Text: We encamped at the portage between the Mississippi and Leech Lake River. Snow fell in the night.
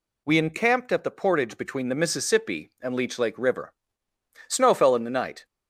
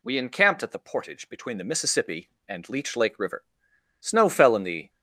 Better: first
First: none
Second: stops before "night"; at 4.8 s

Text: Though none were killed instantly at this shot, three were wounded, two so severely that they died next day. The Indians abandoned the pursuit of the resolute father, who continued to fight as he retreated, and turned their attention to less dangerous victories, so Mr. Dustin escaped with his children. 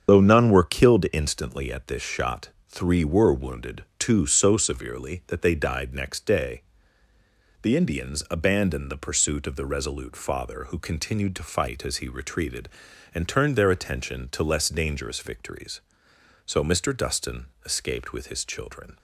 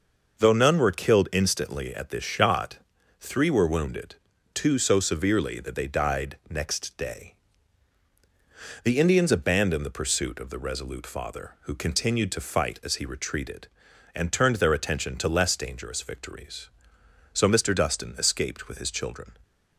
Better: second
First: loses the start of "Though"; at 0.0 s; 60 ms // starts louder than the rest; strong; until 1.1 s; 8 dB // pauses between "Dustin" and "escaped"; slight; at 17.4 s; 0.18 s long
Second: none

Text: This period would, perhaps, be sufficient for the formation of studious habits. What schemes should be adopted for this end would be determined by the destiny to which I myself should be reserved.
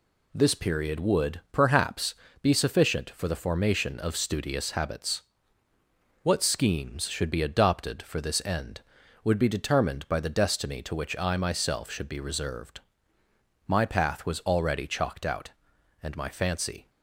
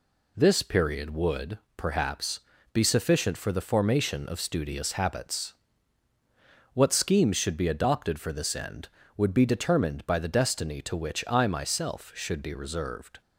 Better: second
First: goes on to say "My path was already chalked out and my fancy"; strong; from 13.6 s on; 3.2 s long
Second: none

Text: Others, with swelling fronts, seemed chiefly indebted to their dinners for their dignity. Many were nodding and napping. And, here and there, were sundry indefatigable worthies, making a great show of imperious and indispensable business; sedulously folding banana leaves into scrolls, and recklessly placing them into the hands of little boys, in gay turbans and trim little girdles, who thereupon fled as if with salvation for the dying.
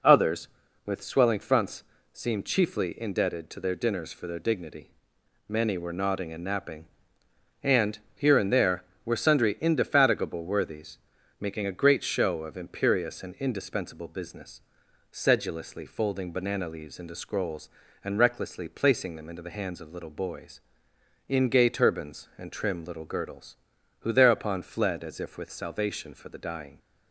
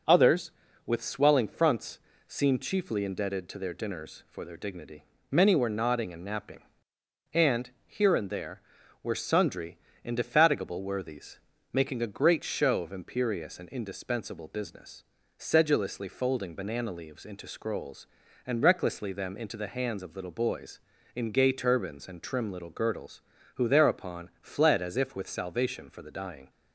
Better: first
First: none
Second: pauses between "sundry" and "indefatigable"; slight; at 9.7 s; 0.26 s long // skips "placing"; at 19.1 s

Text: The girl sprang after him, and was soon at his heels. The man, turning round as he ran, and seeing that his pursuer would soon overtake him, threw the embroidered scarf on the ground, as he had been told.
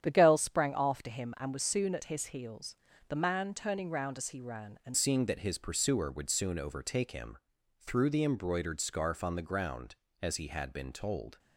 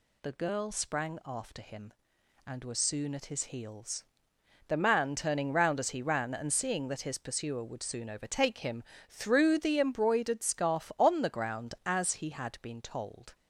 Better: second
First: starts louder than the rest; strong; until 1.0 s; 9.5 dB // changes voice at "seeing"; from 4.9 s on; 6.4 s long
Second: none

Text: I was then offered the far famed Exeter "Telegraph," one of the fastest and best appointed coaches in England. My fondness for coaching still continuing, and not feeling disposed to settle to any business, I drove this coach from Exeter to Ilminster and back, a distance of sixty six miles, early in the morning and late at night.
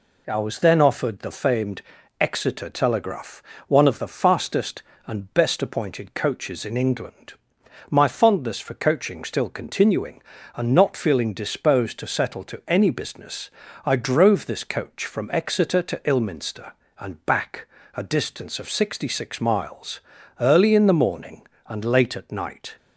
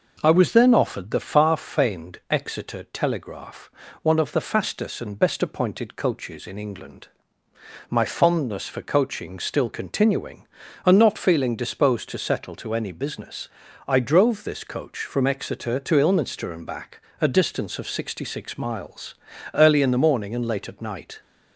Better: second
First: skips "far"; at 1.3 s // pauses between "famed" and "Exeter"; at 1.8 s; 0.38 s long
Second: none

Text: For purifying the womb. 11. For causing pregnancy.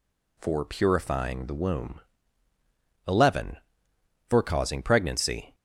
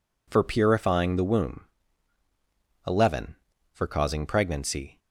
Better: neither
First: none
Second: none

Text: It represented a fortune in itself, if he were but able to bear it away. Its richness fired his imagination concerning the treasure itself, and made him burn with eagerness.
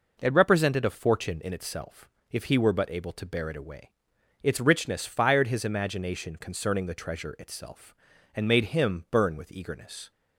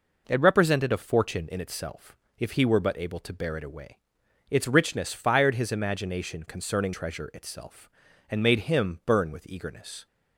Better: first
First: none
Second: skips "the"; at 6.9 s

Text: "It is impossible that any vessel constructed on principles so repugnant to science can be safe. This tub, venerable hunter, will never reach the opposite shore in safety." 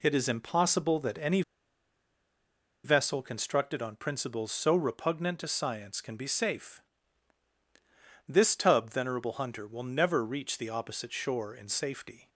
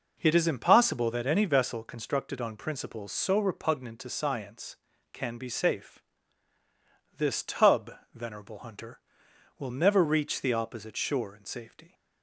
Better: second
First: pauses between "any" and "vessel"; strong; at 1.4 s; 1.4 s long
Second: none

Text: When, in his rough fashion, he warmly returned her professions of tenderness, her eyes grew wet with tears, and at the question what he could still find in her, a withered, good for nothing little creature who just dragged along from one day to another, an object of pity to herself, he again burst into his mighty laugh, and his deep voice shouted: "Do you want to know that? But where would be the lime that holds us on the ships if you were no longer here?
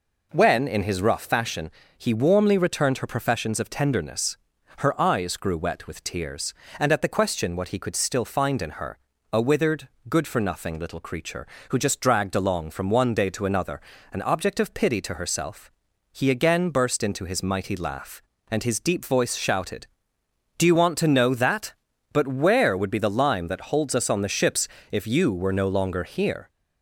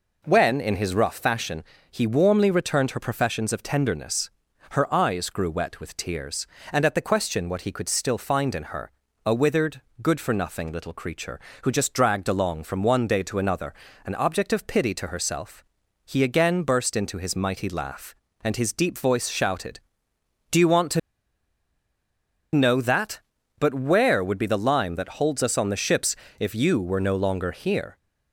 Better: first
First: pauses between "ships" and "if"; slight; at 24.6 s; 0.24 s long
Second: pauses between "to" and "know"; strong; at 20.9 s; 1.5 s long // pauses between "ships" and "if"; slight; at 26.1 s; 0.24 s long

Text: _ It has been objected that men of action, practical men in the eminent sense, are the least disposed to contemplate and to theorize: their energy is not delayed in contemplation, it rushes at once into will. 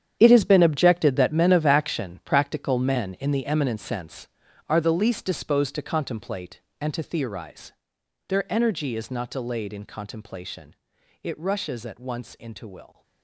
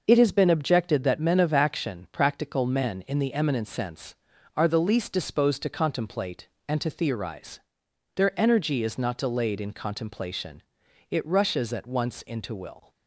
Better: second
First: gets quieter; strong; throughout; 13.5 dB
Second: none

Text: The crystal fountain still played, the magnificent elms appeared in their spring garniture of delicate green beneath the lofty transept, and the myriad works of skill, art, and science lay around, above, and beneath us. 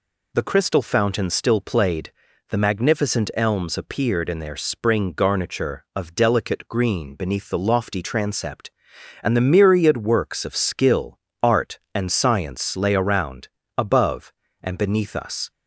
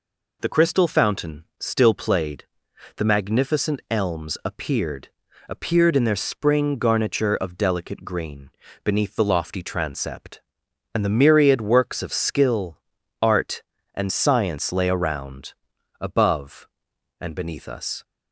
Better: first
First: none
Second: says "appeared" twice; at 5.4 s // pauses between "green" and "beneath"; slight; at 8.5 s; 0.34 s long

